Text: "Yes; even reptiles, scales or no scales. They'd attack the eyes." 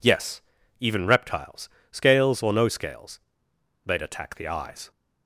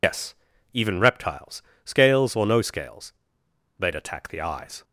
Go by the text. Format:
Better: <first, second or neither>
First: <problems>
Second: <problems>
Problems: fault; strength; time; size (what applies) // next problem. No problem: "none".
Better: first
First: none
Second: loses the start of "Yes"; at 0.0 s; 80 ms